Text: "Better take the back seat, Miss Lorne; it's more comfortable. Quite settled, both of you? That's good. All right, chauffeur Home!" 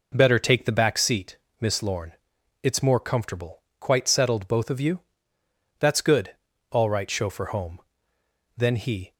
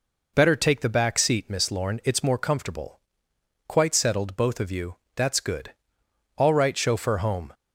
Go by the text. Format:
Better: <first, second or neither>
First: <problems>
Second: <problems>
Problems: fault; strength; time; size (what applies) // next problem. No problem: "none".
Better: second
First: goes on to say "Then he"; from 8.5 s on; 0.58 s long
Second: none